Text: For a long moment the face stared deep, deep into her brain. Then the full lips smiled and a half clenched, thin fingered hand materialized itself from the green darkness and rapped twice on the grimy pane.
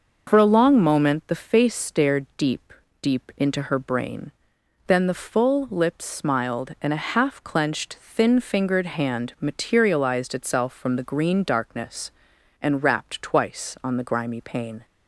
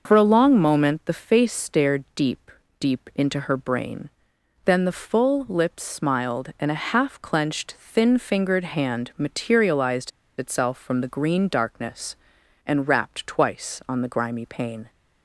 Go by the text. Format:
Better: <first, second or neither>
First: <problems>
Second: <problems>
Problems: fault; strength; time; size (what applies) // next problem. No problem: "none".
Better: first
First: none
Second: pauses between "materialized" and "itself"; slight; at 10.1 s; 0.29 s long